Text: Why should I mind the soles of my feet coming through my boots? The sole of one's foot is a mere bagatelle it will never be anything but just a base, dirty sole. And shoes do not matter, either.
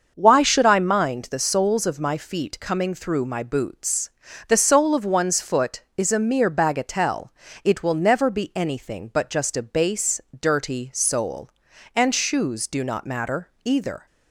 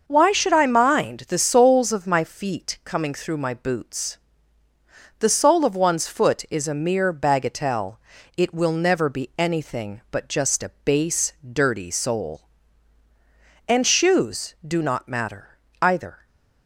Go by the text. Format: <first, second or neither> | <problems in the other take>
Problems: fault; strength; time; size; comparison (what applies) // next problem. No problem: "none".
neither | starts louder than the rest; the same in both // pauses between "bagatelle" and "it"; the same in both